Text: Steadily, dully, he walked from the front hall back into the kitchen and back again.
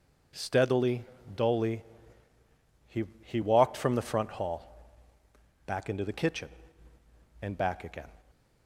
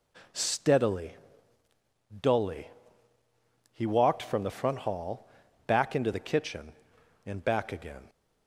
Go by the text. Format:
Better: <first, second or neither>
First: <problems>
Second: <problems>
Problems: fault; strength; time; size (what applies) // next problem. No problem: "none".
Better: second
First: says "he" twice; at 3.2 s // pauses between "hall" and "back"; noticeable; at 4.9 s; 0.72 s long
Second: pauses between "hall" and "back"; at 5.2 s; 0.38 s long